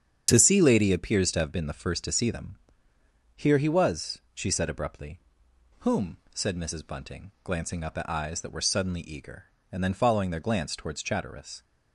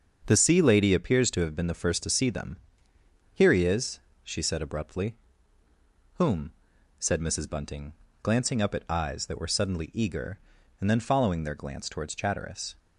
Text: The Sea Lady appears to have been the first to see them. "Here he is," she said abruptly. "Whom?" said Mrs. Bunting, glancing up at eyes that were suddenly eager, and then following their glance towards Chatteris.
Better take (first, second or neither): second